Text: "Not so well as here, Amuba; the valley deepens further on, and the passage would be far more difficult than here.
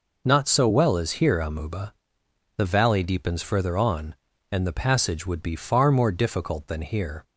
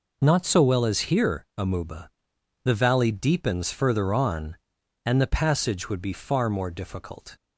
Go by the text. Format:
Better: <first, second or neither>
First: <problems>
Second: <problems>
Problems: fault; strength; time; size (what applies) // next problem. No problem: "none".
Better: first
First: none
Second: stops before "than here"; at 7.3 s